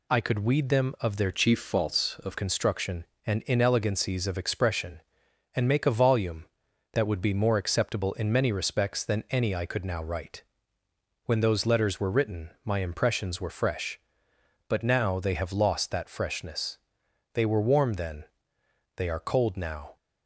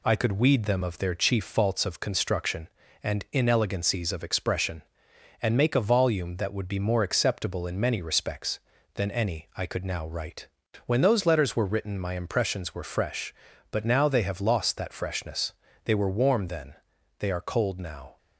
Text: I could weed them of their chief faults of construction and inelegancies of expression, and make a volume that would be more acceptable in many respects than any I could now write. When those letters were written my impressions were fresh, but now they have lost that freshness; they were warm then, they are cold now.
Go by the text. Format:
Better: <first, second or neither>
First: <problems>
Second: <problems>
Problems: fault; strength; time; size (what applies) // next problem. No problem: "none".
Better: second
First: changes voice from "chief" to "of"; from 1.3 to 2.3 s; 1.0 s long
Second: none